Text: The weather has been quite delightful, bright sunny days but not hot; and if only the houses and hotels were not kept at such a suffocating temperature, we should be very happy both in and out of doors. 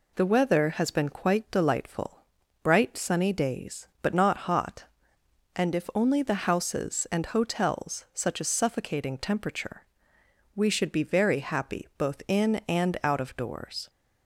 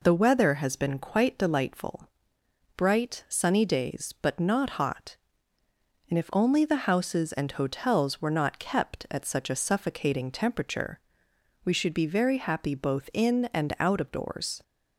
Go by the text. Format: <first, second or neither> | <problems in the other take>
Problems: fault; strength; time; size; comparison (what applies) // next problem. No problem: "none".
second | skips "were not kept at"; at 8.0 s